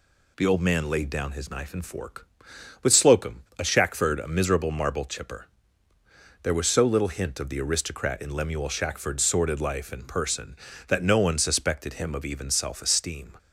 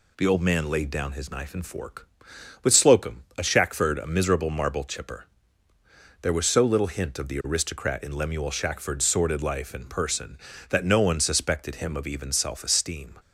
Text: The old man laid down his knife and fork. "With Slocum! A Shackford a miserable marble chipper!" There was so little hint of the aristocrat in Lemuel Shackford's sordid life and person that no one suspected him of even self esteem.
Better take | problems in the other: neither | none

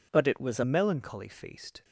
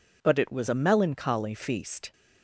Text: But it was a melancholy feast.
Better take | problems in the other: second | changes voice at "melancholy"; from 0.6 s on; 1.2 s long

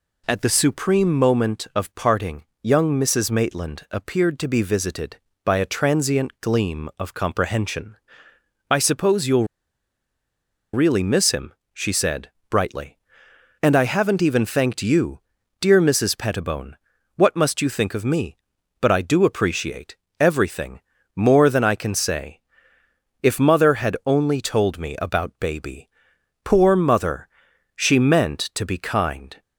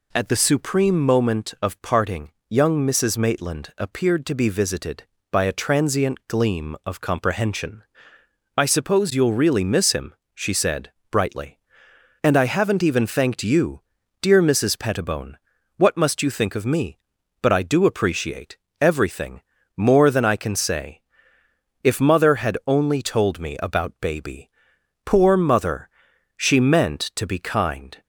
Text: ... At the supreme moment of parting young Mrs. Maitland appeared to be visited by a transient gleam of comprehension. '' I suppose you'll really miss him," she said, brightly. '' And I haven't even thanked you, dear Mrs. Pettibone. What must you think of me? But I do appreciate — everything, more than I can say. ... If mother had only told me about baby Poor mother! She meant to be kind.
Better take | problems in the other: second | pauses between "parting" and "young"; slight; at 2.4 s; 0.18 s long; slight in the second // pauses between "you'll" and "really"; strong; at 9.4 s; 1.2 s long // pauses between "baby" and "Poor"; noticeable; at 25.8 s; 0.56 s long; noticeable in the second

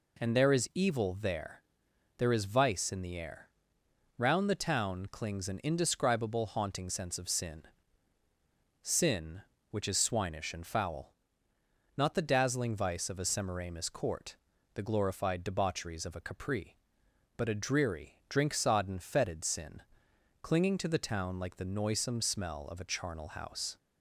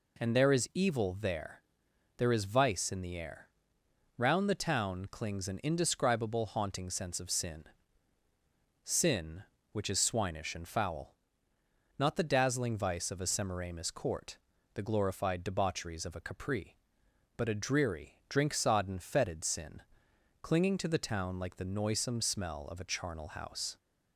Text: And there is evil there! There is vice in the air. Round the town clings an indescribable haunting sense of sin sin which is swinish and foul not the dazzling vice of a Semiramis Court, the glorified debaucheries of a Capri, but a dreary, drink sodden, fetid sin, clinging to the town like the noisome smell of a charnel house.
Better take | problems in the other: neither | pauses between "sin" and "sin"; the same in both // pauses between "foul" and "not"; noticeable; the same in both

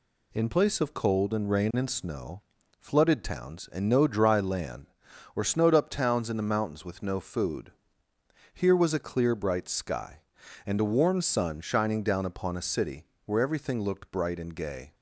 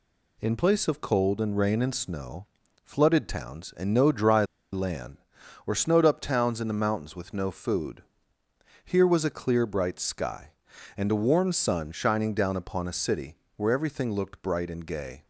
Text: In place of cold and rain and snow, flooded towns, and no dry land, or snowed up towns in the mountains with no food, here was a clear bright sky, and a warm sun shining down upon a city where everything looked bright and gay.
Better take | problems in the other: first | pauses between "dry" and "land"; slight; at 4.4 s; 0.27 s long // pauses between "city" and "where"; slight; at 13.3 s; 0.22 s long; slight in the first

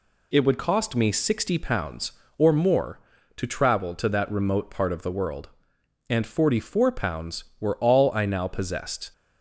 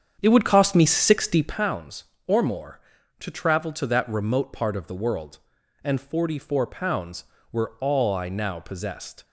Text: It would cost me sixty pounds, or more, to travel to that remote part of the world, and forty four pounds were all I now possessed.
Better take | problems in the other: first | starts louder than the rest; strong; until 1.7 s; 8 dB

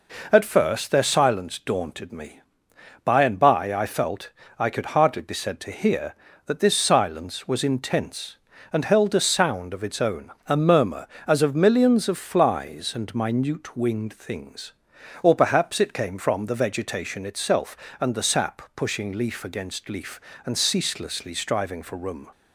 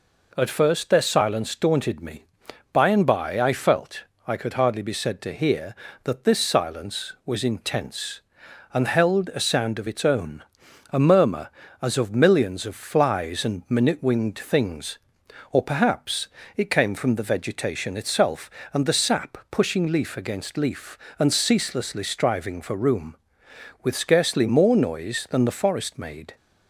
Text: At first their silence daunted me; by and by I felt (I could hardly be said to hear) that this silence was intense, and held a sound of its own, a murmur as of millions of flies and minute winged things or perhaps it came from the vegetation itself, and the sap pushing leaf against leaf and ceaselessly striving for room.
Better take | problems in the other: first | pauses between "perhaps" and "it"; slight; at 16.2 s; 0.28 s long // goes on to say "With scarcely more noise than the forest made"; strong; from 23.8 s on; 2.5 s long

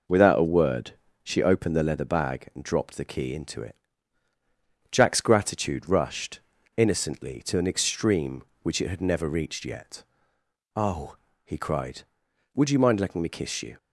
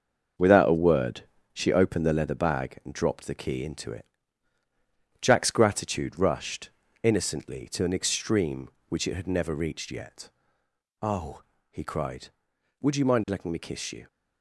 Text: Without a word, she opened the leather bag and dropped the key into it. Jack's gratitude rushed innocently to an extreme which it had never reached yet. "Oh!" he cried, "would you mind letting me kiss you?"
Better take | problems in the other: first | gets quieter; throughout; 7 dB // pauses between "rushed" and "innocently"; slight; at 6.6 s; 0.34 s long; also in the first

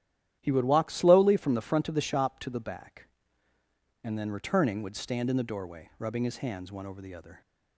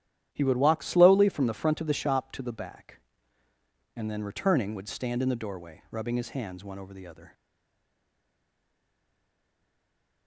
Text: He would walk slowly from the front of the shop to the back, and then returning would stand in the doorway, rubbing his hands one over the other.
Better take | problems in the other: first | starts louder than the rest; strong; until 1.3 s; 11 dB; strong in the first // stays silent after the last word; strong; from 7.3 s on; 2.9 s long

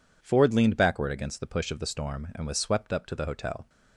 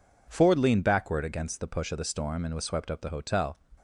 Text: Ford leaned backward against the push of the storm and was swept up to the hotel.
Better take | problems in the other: first | skips "to"; at 2.9 s

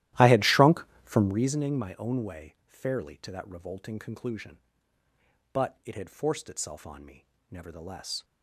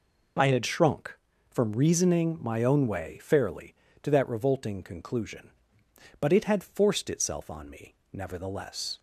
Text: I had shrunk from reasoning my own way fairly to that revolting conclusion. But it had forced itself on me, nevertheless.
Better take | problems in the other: second | starts louder than the rest; strong; until 1.6 s; 15 dB

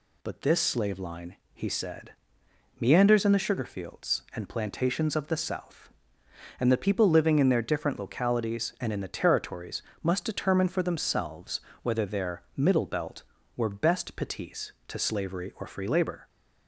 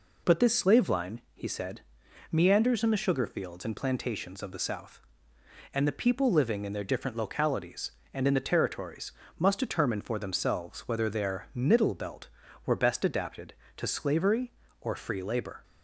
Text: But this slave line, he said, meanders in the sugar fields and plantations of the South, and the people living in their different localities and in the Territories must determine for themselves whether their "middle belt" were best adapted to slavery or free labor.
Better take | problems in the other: second | pauses between "Territories" and "must"; slight; at 9.8 s; 0.22 s long; slight in the second // pauses between "themselves" and "whether"; slight; at 11.6 s; 0.20 s long // says "petits" for "adapted"; at 14.1 s

